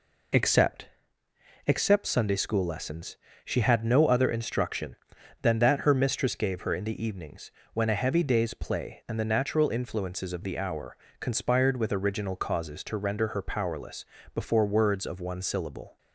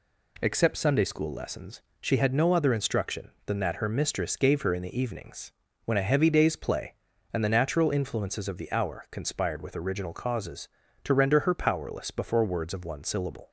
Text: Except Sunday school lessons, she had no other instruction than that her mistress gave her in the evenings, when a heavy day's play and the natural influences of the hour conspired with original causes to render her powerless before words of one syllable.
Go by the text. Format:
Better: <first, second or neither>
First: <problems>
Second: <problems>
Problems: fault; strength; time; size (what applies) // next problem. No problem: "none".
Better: second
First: says "Except" twice; at 1.6 s // pauses between "hour" and "conspired"; slight; at 10.9 s; 0.24 s long // pauses between "powerless" and "before"; slight; at 14.0 s; 0.28 s long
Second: none